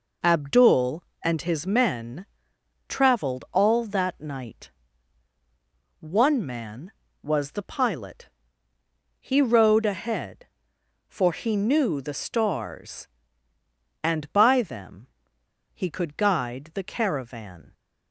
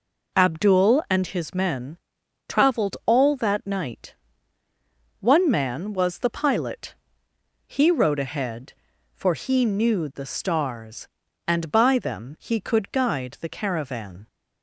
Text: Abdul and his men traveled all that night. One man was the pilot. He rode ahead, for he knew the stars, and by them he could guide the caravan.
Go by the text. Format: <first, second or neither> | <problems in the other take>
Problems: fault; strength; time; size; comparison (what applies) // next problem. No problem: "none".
second | pauses between "men" and "traveled"; noticeable; at 2.2 s; 0.64 s long; noticeable in the second // pauses between "them" and "he"; noticeable; at 15.0 s; 0.67 s long